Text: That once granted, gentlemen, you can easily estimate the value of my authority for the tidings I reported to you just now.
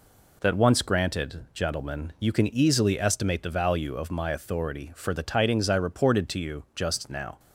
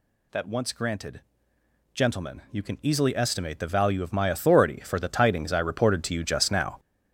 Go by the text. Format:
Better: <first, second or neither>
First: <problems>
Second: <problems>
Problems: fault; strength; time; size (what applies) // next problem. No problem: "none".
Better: first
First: none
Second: gets louder; strong; throughout; 8.5 dB